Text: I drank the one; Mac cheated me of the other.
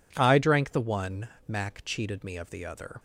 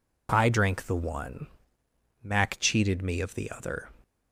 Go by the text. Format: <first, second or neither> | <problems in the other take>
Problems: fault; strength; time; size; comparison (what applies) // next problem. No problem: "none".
neither | none